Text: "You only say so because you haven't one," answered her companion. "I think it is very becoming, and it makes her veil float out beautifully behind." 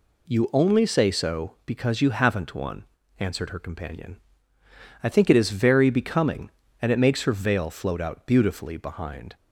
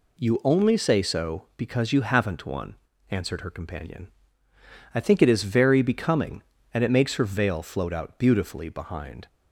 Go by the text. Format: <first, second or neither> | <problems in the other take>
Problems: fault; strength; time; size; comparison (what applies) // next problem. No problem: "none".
neither | none